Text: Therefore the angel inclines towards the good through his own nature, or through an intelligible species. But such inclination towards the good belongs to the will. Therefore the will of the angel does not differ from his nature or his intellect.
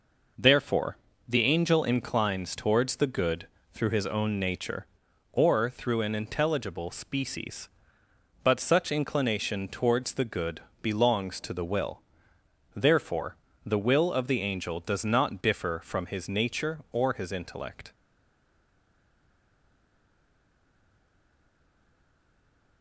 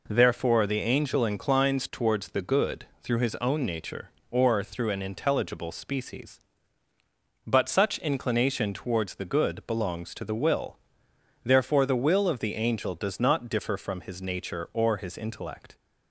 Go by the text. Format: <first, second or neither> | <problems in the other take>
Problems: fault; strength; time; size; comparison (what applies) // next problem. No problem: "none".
second | pauses between "Therefore" and "the"; slight; at 0.9 s; 0.30 s long // pauses between "good" and "through"; slight; at 3.4 s; 0.24 s long; slight in the second // pauses between "good" and "belongs"; slight; at 10.5 s; 0.22 s long // pauses between "Therefore" and "the"; slight; at 13.3 s; 0.30 s long // stays silent after the last word; strong; from 17.9 s on; 4.9 s long